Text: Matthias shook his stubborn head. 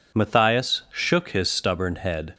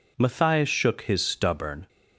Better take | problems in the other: first | stops before "head"; at 1.8 s

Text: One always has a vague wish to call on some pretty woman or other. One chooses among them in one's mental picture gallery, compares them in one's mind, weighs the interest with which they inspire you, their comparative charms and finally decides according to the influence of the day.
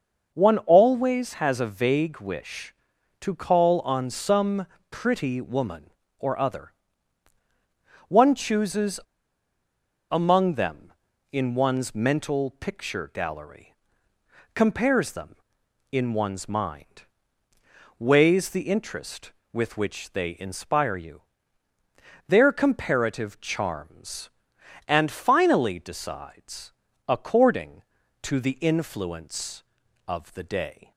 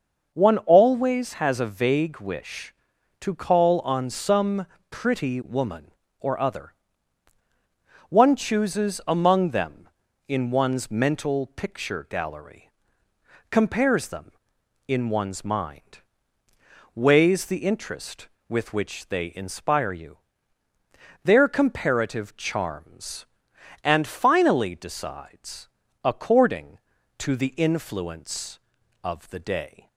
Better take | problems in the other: second | starts louder than the rest; noticeable; until 1.3 s; 6 dB; noticeable in the second // pauses between "some" and "pretty"; slight; at 4.6 s; 0.24 s long; slight in the second // pauses between "chooses" and "among"; at 9.0 s; 1.0 s long // pauses between "decides" and "according"; slight; at 26.7 s; 0.36 s long; slight in the second

